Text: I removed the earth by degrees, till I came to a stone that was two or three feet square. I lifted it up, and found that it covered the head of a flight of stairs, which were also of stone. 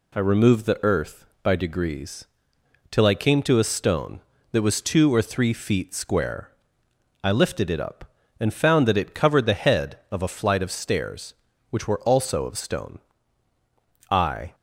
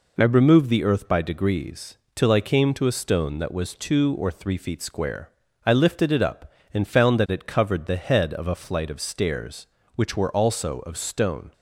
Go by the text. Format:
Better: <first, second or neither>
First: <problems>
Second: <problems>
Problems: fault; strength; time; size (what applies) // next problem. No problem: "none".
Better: second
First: goes on to say "I"; slight; from 14.1 s on; 0.44 s long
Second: none